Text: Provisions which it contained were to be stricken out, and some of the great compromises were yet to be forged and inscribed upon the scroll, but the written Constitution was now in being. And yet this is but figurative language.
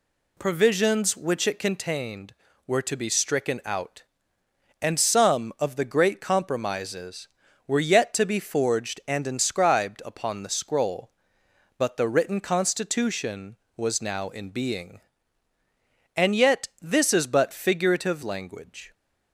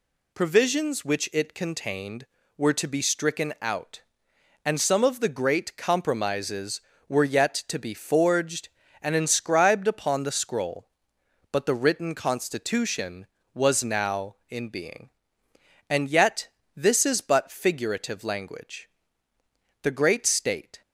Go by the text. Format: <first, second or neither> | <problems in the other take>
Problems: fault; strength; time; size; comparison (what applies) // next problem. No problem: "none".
first | pauses between "yet" and "this"; slight; at 16.4 s; 0.28 s long // goes on to say "The great state"; noticeable; from 19.8 s on; 0.98 s long